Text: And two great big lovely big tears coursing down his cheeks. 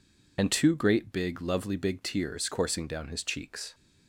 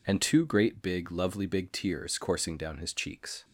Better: second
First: loses the start of "And"; at 0.3 s; 35 ms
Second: none

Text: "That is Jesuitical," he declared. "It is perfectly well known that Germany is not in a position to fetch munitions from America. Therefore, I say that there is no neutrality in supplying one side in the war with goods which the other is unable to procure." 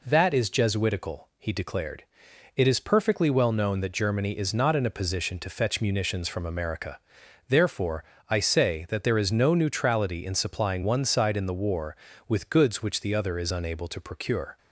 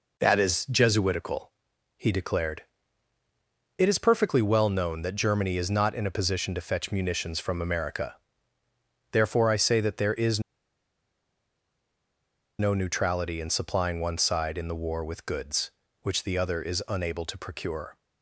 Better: first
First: none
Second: pauses between "is" and "no"; strong; at 10.3 s; 2.1 s long

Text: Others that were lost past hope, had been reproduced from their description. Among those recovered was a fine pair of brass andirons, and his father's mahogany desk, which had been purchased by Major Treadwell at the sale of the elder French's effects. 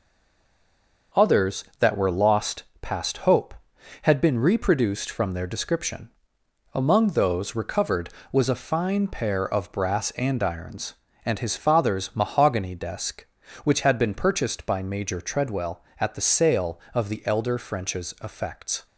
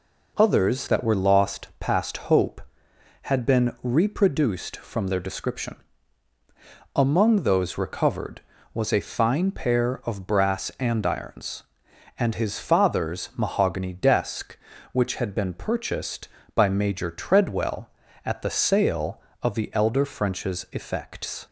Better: second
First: stays silent before the first word; until 1.1 s; 1.1 s long // pauses between "lost" and "past"; slight; at 2.6 s; 0.16 s long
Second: none

